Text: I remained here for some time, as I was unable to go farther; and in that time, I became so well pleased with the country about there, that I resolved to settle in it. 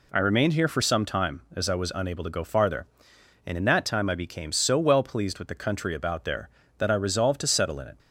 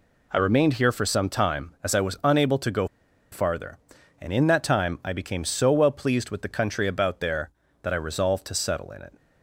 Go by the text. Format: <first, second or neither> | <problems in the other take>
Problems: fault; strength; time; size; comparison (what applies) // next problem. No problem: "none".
first | pauses between "go" and "farther"; noticeable; at 2.8 s; 0.46 s long